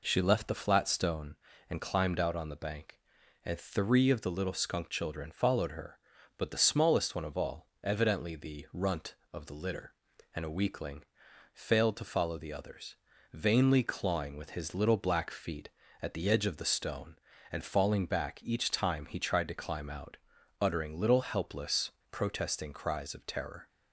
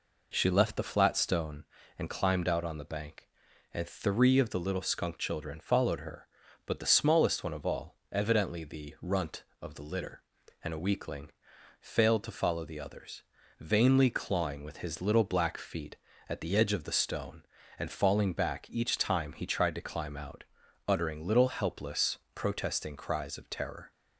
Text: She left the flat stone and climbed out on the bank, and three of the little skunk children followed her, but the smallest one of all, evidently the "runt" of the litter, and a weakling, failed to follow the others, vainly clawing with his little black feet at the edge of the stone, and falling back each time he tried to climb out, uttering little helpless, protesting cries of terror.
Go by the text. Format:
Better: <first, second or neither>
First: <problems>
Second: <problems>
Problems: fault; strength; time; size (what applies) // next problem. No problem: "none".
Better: neither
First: none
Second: none